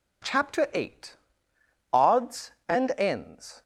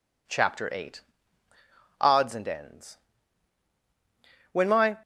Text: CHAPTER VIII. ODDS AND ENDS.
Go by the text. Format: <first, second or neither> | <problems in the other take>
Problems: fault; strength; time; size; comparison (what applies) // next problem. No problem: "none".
first | goes on to say "When my"; slight; from 4.5 s on; 0.46 s long